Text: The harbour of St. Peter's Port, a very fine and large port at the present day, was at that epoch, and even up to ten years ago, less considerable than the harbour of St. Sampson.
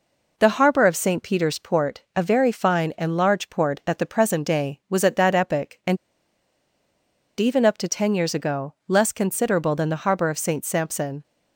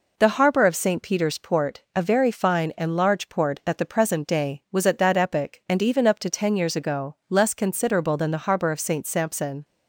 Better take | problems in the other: second | pauses between "and" and "even"; strong; at 5.9 s; 1.4 s long

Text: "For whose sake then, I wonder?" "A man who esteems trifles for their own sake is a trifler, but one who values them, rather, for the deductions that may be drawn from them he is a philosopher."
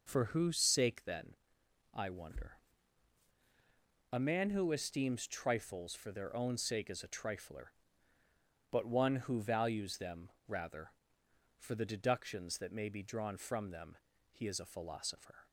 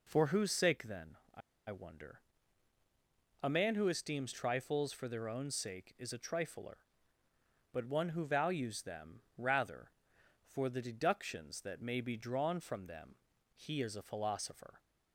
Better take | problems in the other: first | pauses between "I" and "wonder"; slight; at 1.4 s; 0.29 s long // pauses between "them" and "he"; at 13.1 s; 0.40 s long; slight in the first

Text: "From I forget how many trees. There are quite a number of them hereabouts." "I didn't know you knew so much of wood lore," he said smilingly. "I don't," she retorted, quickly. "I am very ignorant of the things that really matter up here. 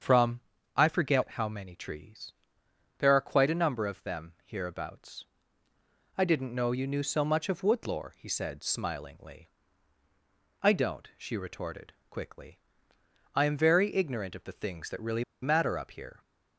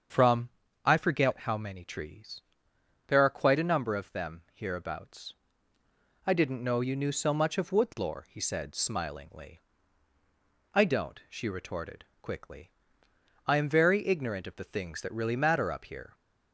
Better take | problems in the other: second | starts louder than the rest; strong; until 1.3 s; 7 dB; strong in the second // pauses between "From" and "I"; slight; at 0.4 s; 0.34 s long; slight in the second // pauses between "really" and "matter"; slight; at 15.2 s; 0.20 s long

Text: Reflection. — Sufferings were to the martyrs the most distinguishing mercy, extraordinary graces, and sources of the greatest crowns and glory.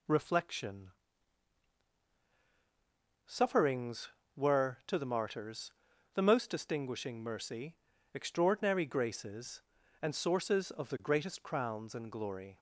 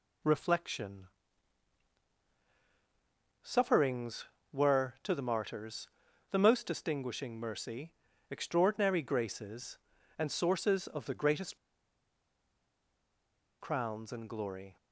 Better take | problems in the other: first | pauses between "martyrs" and "the"; at 5.8 s; 0.44 s long; also in the first // pauses between "greatest" and "crowns"; strong; at 11.5 s; 2.0 s long

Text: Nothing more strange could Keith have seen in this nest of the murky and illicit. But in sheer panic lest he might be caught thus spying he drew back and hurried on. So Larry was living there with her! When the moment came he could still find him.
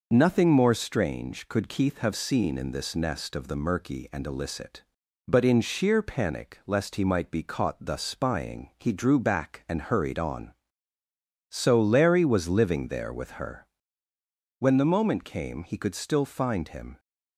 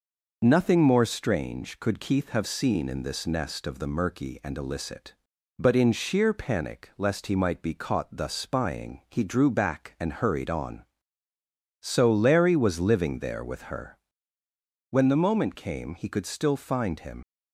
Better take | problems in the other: first | leaves "him" unfinished; at 17.2 s; 75 ms

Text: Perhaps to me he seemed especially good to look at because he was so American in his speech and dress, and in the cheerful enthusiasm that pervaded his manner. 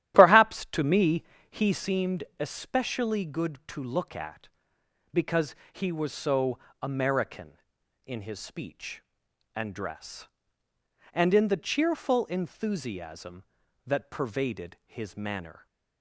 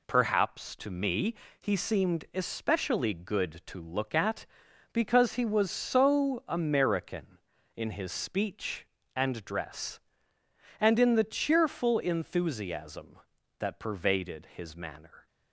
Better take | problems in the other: second | starts louder than the rest; strong; until 1.9 s; 12 dB // pauses between "me" and "he"; slight; at 1.2 s; 0.26 s long; slight in the second // pauses between "seemed" and "especially"; slight; at 2.2 s; 0.16 s long // pauses between "because" and "he"; slight; at 5.5 s; 0.20 s long // pauses between "so" and "American"; slight; at 6.5 s; 0.24 s long

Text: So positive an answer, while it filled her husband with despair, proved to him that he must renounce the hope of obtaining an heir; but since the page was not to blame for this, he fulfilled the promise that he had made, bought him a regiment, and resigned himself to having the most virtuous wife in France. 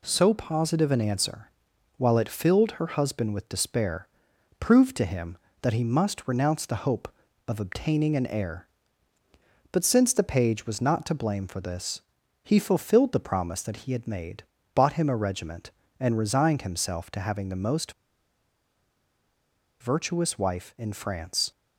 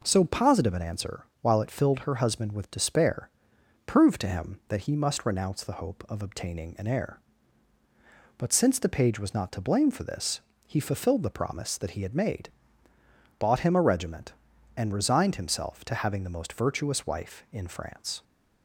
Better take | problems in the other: second | pauses between "most" and "virtuous"; strong; at 17.9 s; 1.8 s long

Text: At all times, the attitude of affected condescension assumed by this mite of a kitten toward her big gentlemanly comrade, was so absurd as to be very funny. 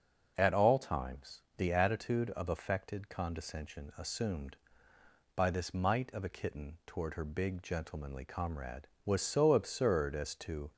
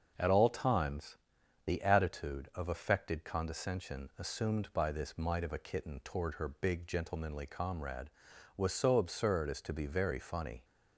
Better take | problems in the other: second | starts louder than the rest; until 1.3 s; 6.5 dB; also in the second // stops before "be very funny"; at 10.7 s

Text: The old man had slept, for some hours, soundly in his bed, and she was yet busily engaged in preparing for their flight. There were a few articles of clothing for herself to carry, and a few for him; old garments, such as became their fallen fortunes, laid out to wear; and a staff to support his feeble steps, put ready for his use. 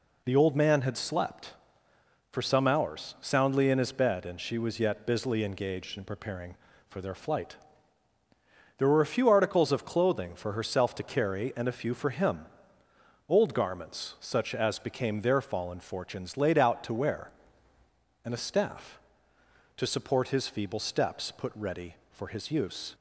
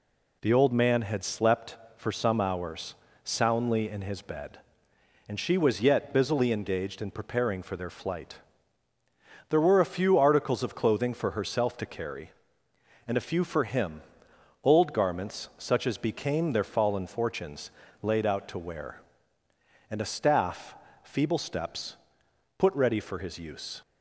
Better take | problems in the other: first | skips "to support his"; at 20.8 s

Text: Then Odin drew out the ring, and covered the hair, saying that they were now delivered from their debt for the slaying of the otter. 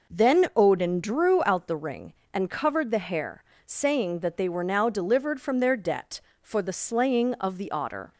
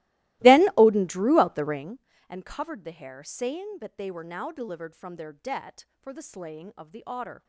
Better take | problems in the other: first | starts louder than the rest; strong; until 1.9 s; 18.5 dB

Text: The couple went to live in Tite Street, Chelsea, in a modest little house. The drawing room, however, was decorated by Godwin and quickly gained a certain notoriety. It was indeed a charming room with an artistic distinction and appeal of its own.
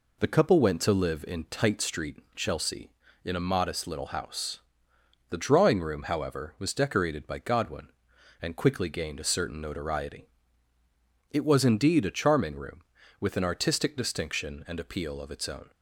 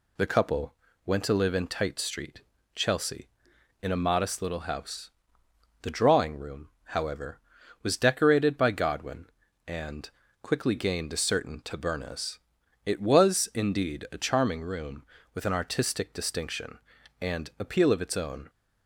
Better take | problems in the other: first | pauses between "couple" and "went"; slight; at 0.7 s; 0.32 s long // pauses between "and" and "quickly"; slight; at 10.0 s; 0.32 s long // says "tabernas" for "notoriety"; at 11.6 s

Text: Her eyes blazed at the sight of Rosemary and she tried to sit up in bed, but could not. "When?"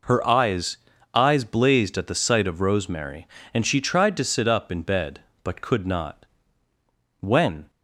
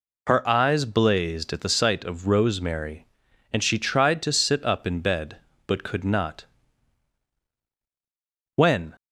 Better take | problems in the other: second | says "eyes" twice; at 1.1 s

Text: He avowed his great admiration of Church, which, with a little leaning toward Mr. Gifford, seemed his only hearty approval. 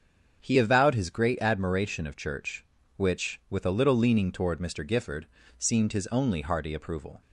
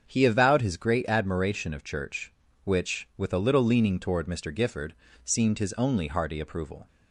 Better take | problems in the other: neither | starts louder than the rest; strong; the same in both

